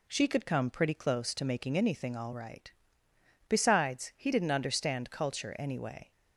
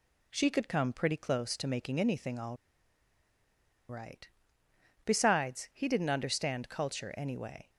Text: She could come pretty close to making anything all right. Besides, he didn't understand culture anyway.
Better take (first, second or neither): first